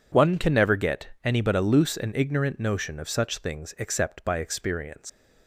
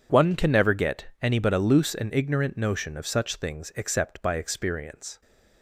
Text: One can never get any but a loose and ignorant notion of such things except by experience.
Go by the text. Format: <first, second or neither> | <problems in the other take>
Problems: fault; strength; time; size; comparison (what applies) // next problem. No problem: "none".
second | pauses between "get" and "any"; slight; at 1.0 s; 0.16 s long; slight in the second // leaves "experience" unfinished; at 5.0 s; 135 ms